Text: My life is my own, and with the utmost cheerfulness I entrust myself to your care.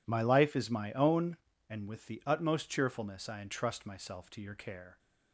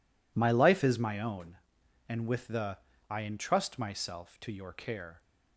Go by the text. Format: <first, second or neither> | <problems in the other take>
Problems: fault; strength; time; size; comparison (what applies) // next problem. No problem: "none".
first | skips "utmost cheerfulness"; at 2.9 s